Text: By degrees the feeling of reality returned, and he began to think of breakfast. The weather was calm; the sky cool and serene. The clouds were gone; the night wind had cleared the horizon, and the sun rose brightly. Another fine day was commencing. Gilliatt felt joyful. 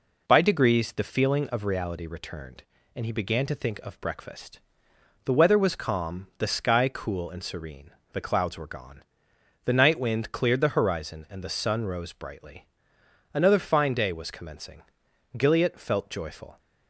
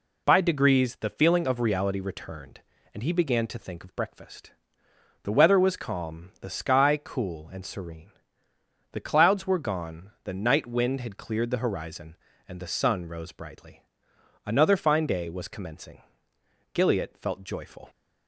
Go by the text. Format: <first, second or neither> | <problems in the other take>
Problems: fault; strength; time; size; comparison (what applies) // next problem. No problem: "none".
second | skips "had"; at 10.3 s